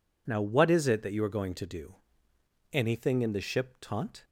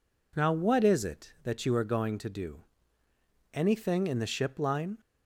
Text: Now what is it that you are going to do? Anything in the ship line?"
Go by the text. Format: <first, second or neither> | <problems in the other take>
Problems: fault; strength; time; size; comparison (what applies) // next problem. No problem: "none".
second | says "taunt" for "line"; at 3.7 s